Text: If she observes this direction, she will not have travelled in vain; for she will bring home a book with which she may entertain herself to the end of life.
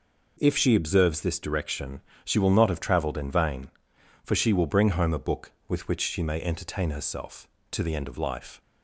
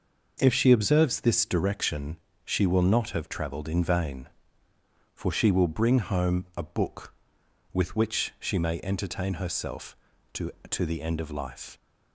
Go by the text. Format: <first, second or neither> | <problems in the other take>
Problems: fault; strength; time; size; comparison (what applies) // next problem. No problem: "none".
first | says "to" twice; at 10.7 s